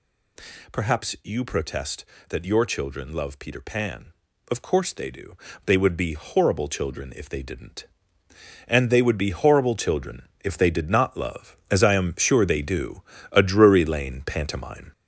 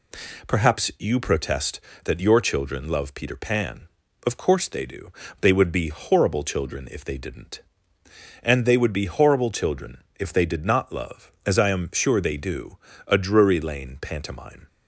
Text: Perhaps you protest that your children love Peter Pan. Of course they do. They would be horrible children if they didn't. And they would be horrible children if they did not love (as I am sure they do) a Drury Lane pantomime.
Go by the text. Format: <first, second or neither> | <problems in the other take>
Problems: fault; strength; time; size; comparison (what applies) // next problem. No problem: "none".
second | gets louder; noticeable; throughout; 5.5 dB // pauses between "children" and "if"; slight; at 10.2 s; 0.16 s long; slight in the second